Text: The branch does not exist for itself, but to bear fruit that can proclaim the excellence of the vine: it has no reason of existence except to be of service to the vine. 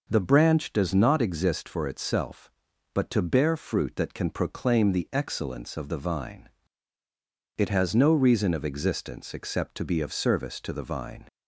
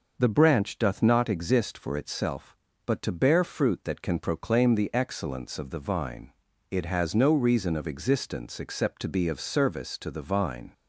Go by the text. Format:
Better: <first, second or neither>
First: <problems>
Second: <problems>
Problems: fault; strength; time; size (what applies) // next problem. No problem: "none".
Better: first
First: none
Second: says "doth" for "does"; at 0.7 s